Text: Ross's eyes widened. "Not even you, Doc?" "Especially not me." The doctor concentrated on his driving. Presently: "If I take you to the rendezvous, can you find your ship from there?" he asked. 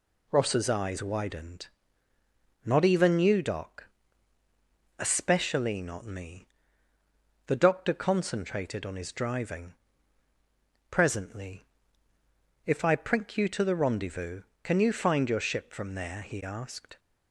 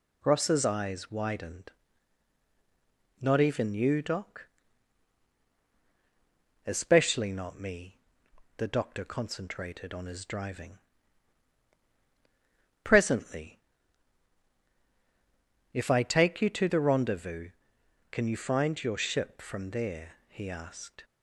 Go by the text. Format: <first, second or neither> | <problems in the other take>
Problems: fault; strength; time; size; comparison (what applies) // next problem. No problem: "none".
second | says "prink" for "take"; at 12.9 s